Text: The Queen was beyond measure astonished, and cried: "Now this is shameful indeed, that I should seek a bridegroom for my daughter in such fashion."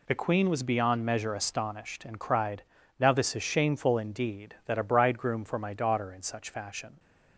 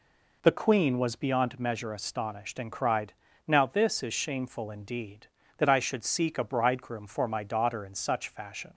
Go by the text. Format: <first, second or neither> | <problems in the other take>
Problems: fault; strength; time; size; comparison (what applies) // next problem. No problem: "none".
second | skips "I should seek"; at 4.7 s